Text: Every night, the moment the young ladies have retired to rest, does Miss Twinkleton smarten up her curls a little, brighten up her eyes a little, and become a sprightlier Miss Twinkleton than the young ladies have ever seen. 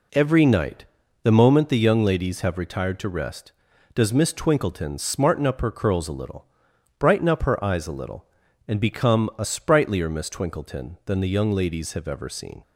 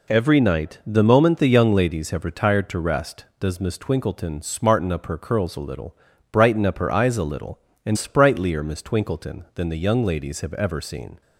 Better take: first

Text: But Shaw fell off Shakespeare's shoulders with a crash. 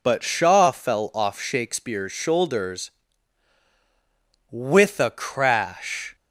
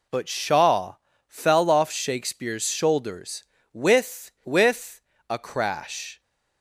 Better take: first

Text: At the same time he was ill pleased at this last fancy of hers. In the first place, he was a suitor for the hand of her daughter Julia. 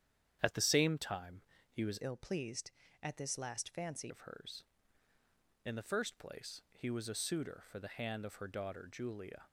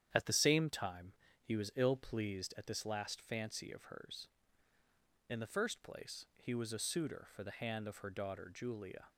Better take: second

